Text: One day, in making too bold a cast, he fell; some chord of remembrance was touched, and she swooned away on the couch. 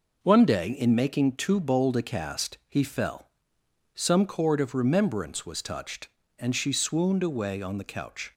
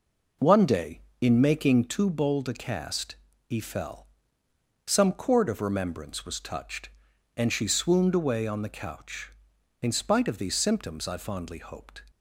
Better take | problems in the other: first | goes on to say "In spite of these symptoms I fondly hoped"; strong; from 9.8 s on; 2.2 s long

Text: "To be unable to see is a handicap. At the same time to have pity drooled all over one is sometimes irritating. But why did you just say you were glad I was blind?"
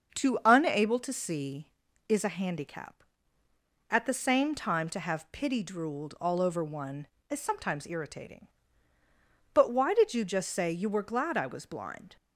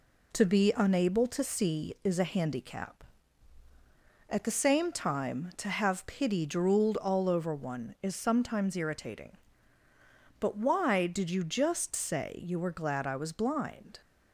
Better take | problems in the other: second | starts louder than the rest; until 1.2 s; 6.5 dB // skips "be"; at 0.4 s

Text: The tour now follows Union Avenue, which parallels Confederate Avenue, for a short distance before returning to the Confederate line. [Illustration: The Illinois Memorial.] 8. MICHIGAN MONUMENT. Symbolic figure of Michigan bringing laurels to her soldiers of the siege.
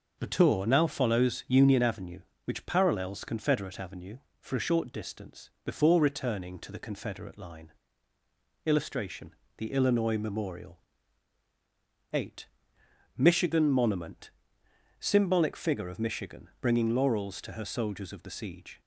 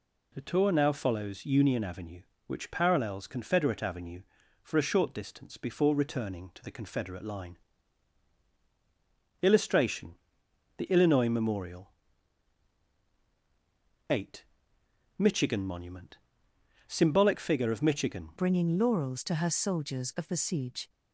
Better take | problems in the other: first | changes voice at "bringing"; from 18.3 s on; 2.5 s long

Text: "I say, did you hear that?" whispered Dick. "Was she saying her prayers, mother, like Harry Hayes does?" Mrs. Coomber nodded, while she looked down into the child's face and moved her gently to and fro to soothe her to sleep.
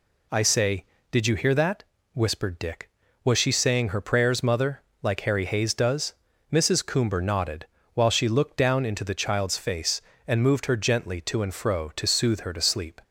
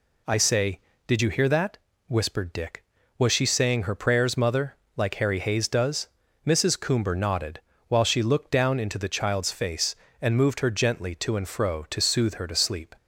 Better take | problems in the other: neither | none

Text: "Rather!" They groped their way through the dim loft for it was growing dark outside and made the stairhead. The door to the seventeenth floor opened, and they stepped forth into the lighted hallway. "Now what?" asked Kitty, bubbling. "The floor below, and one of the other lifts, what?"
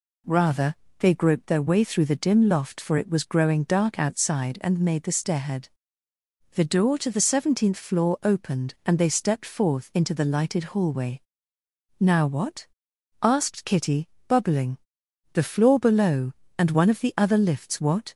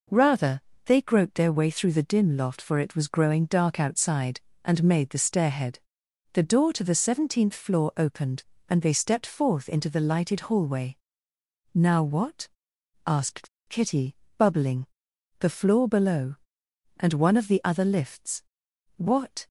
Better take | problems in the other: first | pauses between "asked" and "Kitty"; slight; at 13.4 s; 0.20 s long

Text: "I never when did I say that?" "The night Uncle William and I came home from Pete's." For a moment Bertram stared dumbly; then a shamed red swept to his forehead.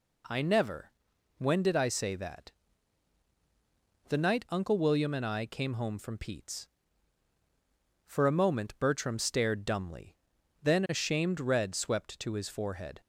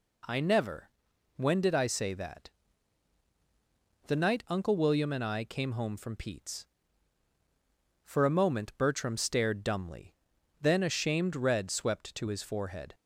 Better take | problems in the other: neither | pauses between "never" and "when"; noticeable; the same in both

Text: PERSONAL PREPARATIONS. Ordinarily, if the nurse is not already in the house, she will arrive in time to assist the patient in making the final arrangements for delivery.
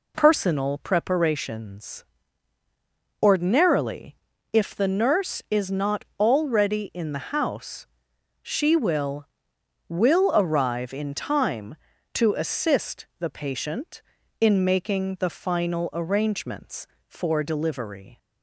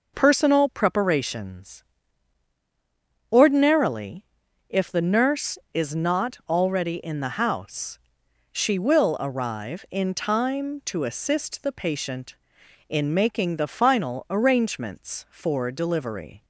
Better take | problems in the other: second | says "will" twice; at 9.8 s

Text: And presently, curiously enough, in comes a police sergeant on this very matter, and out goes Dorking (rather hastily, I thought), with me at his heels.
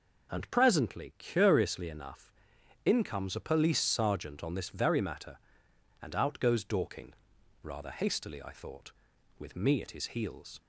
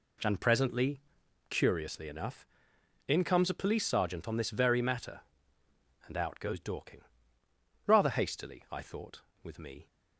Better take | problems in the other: first | stops before "at his heels"; at 9.8 s

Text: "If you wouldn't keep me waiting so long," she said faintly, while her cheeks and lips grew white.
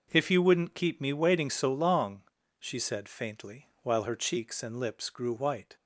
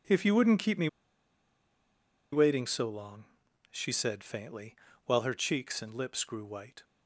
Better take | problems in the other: first | pauses between "me" and "waiting"; strong; at 0.8 s; 1.4 s long

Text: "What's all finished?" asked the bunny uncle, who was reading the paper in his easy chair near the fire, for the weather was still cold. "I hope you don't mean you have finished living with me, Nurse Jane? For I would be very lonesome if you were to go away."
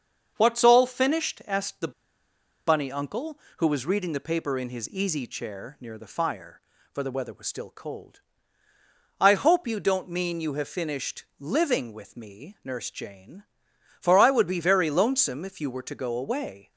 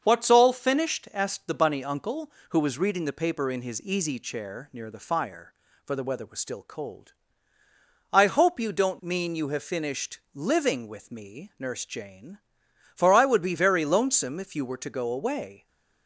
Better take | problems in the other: second | starts louder than the rest; until 1.3 s; 7 dB; also in the second // pauses between "the" and "bunny"; noticeable; at 1.9 s; 0.75 s long // pauses between "finished" and "living"; slight; at 11.2 s; 0.16 s long; slight in the second

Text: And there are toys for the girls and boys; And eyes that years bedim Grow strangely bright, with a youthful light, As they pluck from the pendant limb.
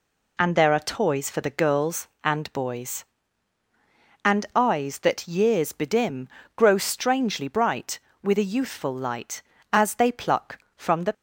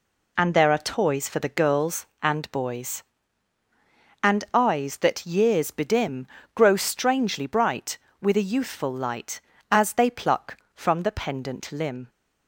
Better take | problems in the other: second | pauses between "bedim" and "Grow"; slight; at 6.2 s; 0.28 s long; slight in the second // stops before "pendant limb"; at 11.1 s

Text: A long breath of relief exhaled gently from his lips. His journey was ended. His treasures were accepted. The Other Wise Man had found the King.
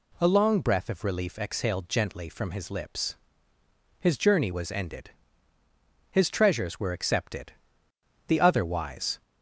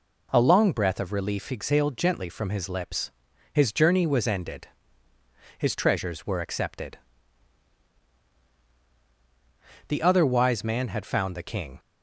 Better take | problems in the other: second | stops before "Man had found the King"; at 9.2 s

